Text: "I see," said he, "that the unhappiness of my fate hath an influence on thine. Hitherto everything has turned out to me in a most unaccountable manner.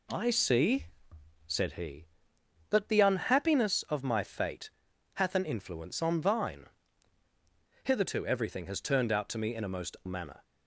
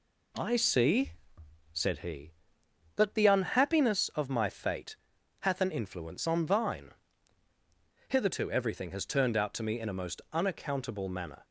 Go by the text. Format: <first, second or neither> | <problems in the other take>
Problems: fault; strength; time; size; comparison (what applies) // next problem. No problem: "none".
second | pauses between "fate" and "hath"; at 4.6 s; 0.44 s long; also in the second // skips "unaccountable"; at 10.0 s